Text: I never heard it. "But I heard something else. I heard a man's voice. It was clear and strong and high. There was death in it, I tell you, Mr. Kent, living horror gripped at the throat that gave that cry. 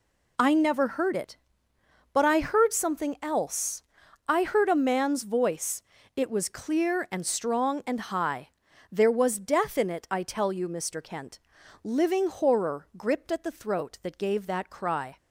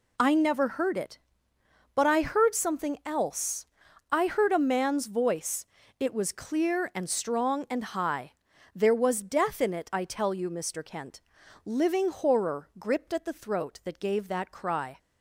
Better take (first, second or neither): neither